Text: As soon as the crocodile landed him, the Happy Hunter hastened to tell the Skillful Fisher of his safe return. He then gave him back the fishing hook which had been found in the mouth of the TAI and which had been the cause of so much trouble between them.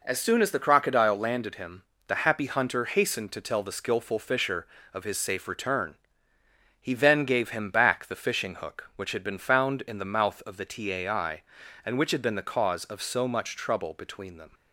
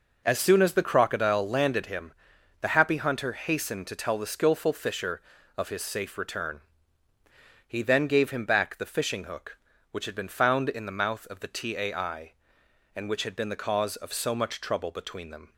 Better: neither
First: none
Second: none

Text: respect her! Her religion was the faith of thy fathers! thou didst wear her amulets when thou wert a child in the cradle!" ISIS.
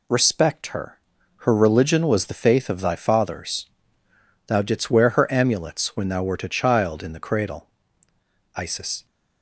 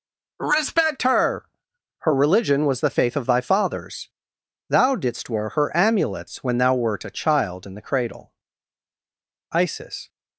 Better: neither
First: none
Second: none

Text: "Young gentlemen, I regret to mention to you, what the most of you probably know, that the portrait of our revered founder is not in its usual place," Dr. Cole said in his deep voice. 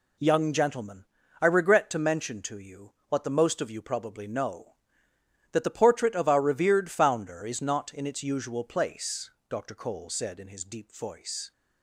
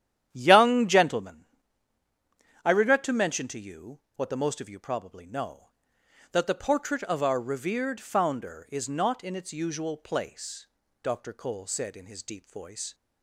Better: first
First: none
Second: starts louder than the rest; strong; until 1.4 s; 10.5 dB

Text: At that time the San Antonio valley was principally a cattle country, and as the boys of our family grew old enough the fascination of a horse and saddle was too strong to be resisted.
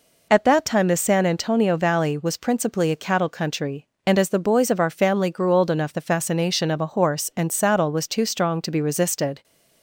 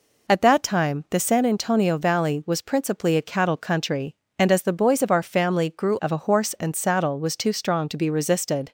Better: first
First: none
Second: skips "old enough the fascination"; at 6.0 s

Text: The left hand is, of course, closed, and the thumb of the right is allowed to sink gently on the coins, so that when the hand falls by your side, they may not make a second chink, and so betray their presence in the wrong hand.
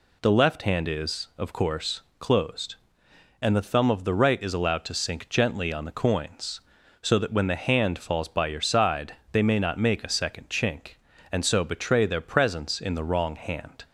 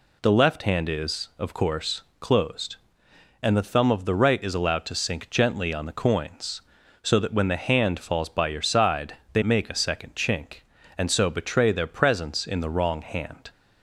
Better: first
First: none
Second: skips "may not"; at 9.4 s

